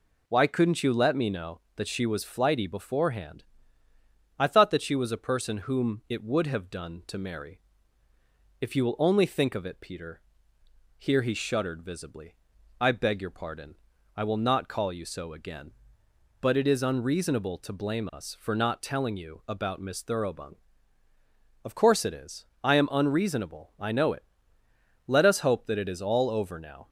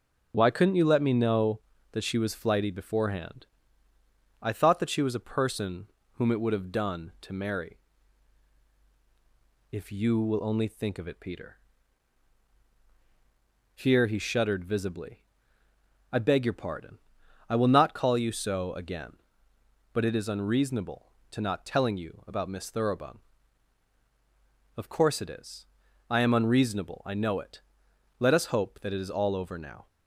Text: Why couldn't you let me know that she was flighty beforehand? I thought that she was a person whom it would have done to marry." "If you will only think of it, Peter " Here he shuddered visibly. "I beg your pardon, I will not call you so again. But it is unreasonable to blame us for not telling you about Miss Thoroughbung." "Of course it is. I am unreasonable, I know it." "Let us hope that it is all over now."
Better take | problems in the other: first | starts louder than the rest; until 1.3 s; 6.5 dB // pauses between "person" and "whom"; slight; at 5.8 s; 0.30 s long // skips "blame us for"; at 21.3 s

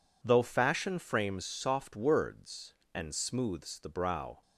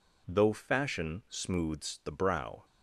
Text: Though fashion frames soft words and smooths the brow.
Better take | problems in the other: first | skips "frames soft words and"; at 1.2 s

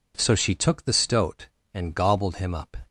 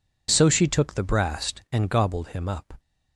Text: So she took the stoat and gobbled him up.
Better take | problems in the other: first | says "brast" for "stoat"; at 1.0 s

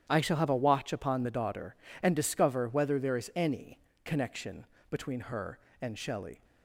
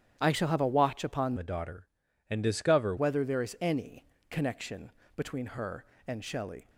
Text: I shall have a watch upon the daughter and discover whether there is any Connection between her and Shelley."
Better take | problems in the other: first | starts louder than the rest; strong; until 1.2 s; 10 dB; strong in the first // changes voice from "the" to "discover"; from 1.3 to 2.9 s; 1.6 s long // pauses between "any" and "Connection"; slight; at 4.0 s; 0.26 s long; slight in the first // pauses between "Connection" and "between"; slight; at 4.9 s; 0.24 s long; slight in the first

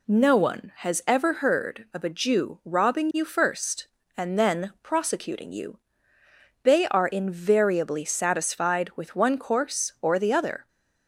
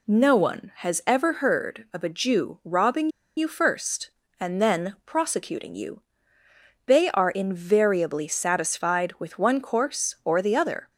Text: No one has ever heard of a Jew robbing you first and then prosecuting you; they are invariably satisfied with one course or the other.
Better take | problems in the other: first | pauses between "robbing" and "you"; slight; at 3.0 s; 0.29 s long

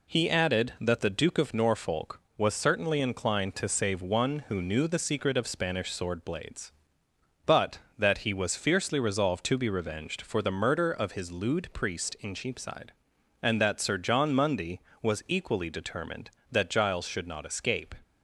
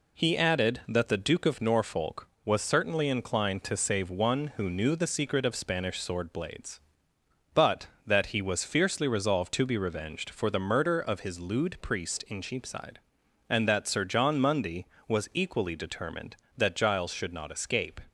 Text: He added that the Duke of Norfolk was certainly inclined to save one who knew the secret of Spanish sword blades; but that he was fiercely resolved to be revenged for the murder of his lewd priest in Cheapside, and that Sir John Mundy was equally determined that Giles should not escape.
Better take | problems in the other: neither | none

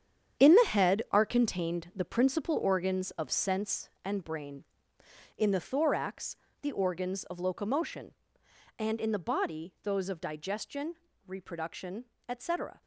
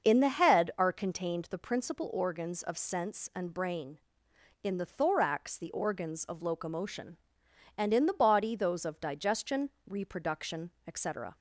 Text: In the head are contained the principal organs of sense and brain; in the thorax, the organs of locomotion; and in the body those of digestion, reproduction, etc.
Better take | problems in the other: second | gets quieter; strong; throughout; 11 dB // starts louder than the rest; strong; until 1.4 s; 9 dB; also in the second

